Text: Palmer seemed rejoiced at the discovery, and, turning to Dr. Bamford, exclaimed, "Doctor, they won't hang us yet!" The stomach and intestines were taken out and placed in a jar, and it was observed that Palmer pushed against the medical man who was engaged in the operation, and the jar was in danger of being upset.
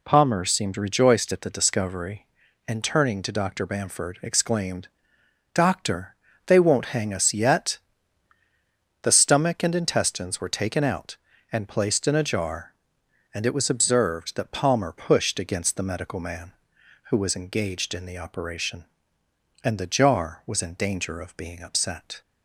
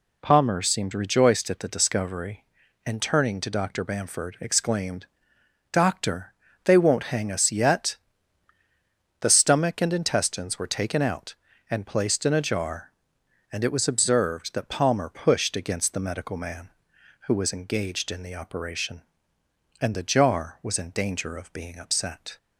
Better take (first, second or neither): neither